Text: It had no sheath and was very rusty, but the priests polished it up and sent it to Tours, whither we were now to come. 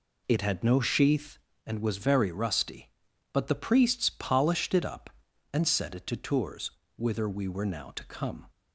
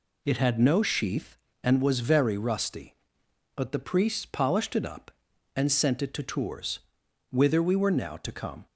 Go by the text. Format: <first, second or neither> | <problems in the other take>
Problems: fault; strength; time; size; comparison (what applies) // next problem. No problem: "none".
second | says "set" for "sent"; at 5.6 s